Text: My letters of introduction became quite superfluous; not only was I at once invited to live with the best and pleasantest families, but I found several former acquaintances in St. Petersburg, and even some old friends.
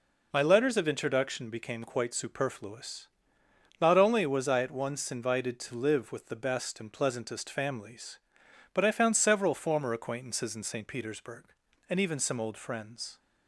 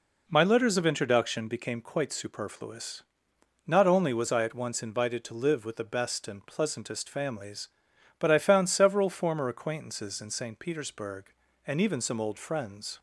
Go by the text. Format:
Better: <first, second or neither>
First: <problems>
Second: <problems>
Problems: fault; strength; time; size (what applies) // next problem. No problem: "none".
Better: neither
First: none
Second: none